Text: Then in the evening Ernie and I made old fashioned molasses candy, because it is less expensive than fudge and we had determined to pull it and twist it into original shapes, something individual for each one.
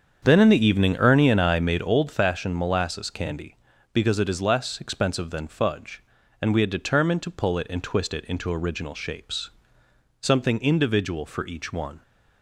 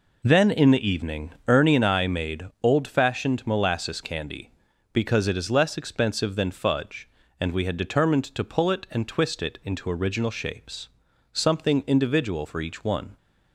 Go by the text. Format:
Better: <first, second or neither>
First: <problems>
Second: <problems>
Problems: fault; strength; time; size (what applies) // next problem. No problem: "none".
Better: second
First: starts louder than the rest; strong; until 1.9 s; 7.5 dB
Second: none